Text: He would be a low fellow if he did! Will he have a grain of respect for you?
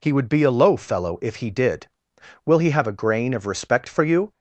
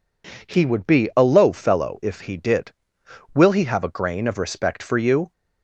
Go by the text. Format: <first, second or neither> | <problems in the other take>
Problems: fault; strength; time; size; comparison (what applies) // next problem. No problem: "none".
neither | none